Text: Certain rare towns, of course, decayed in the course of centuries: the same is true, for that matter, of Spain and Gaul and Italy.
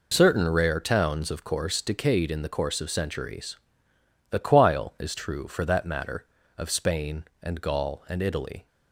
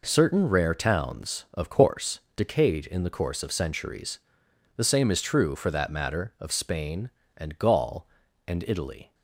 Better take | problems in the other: second | says "quile" for "same"; at 4.3 s

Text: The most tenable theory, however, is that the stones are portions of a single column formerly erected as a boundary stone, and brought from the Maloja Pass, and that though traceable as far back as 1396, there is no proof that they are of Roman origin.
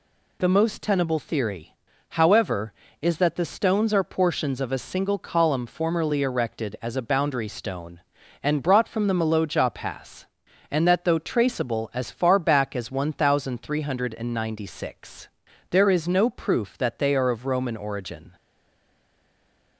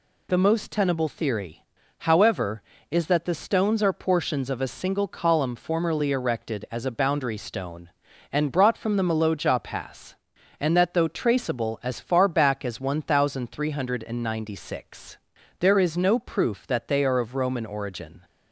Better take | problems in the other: second | stays silent after the last word; noticeable; from 18.3 s on; 1.4 s long

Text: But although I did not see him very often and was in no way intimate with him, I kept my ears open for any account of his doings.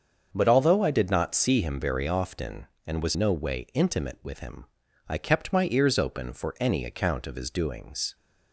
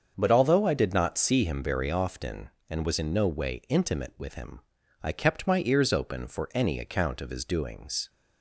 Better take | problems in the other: second | starts louder than the rest; until 1.3 s; 7 dB; also in the second // skips "in"; at 3.1 s

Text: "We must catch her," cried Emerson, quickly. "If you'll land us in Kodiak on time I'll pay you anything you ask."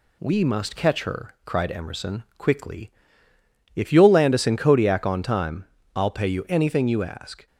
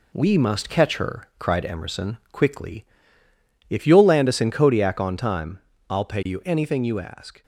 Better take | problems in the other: first | gets quieter; noticeable; throughout; 4.5 dB // pauses between "time" and "I'll"; slight; at 5.5 s; 0.30 s long; slight in the first

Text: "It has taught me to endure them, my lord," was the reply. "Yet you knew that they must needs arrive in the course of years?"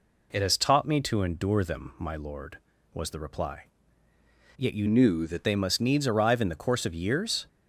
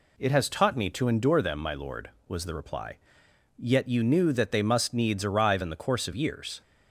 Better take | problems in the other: second | changes voice from "knew" to "that"; from 4.8 to 5.4 s; 0.6 s long

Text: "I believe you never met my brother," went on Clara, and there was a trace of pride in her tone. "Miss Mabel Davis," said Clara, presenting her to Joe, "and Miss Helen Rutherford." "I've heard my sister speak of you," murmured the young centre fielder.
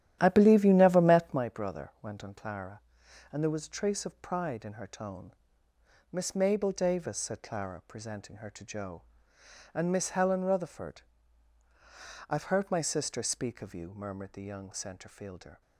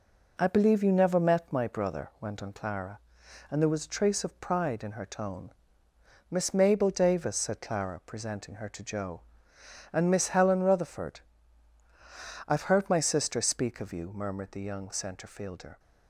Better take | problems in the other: second | starts louder than the rest; strong; until 1.4 s; 11.5 dB

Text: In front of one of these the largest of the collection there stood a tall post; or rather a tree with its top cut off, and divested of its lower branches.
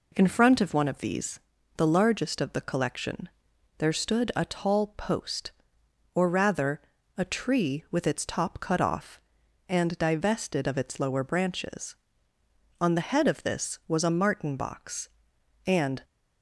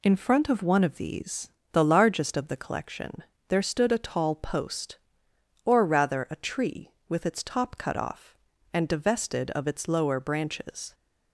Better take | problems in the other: second | pauses between "these" and "the"; at 1.3 s; 0.38 s long; slight in the second // pauses between "collection" and "there"; noticeable; at 3.2 s; 0.50 s long; slight in the second // pauses between "rather" and "a"; slight; at 6.8 s; 0.34 s long // goes on to say "On the head of this was a martin box and"; strong; from 12.7 s on; 3.2 s long

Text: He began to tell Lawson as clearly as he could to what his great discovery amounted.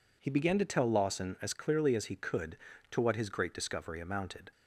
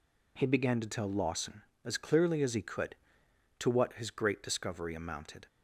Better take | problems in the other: neither | none

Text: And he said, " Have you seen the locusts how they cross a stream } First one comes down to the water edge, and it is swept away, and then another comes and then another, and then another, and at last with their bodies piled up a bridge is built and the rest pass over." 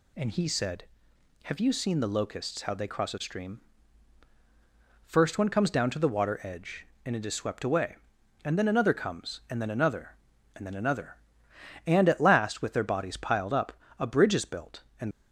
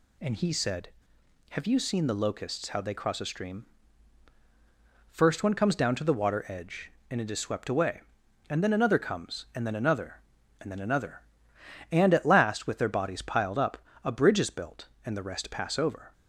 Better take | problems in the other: second | pauses between "up" and "a"; slight; at 13.7 s; 0.26 s long; slight in the second // stops before "the rest pass over"; at 15.1 s

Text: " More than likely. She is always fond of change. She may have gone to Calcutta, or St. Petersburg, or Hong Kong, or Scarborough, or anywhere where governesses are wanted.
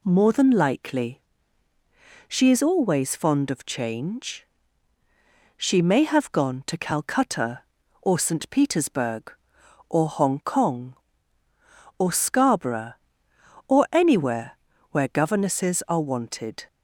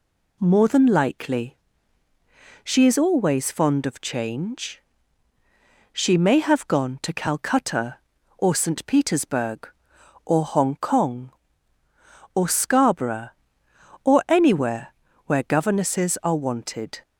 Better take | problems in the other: neither | pauses between "anywhere" and "where"; slight; the same in both

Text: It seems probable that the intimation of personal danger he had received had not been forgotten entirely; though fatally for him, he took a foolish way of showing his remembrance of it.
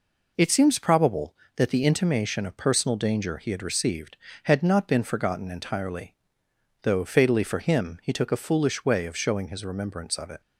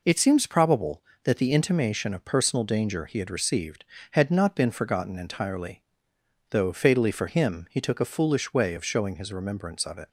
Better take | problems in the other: neither | none

